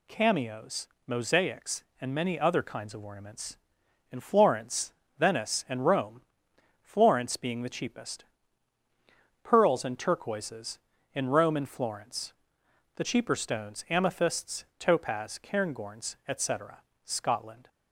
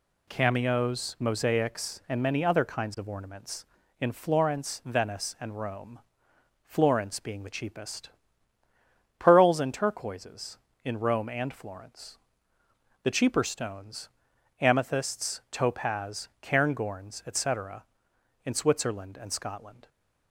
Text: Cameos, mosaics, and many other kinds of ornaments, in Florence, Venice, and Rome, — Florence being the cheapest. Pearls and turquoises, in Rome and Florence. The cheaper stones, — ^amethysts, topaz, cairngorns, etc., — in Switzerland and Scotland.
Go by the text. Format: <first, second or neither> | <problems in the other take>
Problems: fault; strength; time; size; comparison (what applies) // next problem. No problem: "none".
second | skips "in Switzerland and"; at 16.9 s